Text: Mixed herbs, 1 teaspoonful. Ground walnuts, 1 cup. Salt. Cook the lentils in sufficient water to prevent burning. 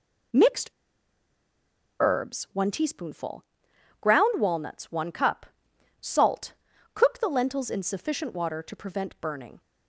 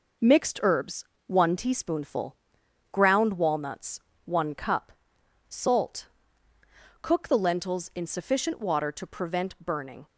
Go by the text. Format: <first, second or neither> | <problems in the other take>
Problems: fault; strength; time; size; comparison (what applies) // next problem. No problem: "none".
second | pauses between "Mixed" and "herbs"; strong; at 0.6 s; 1.3 s long